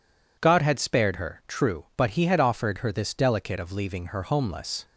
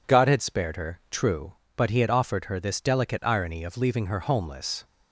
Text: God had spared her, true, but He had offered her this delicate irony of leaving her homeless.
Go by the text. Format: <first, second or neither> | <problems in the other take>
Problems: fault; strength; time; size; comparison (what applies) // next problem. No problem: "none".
second | skips "irony"; at 3.5 s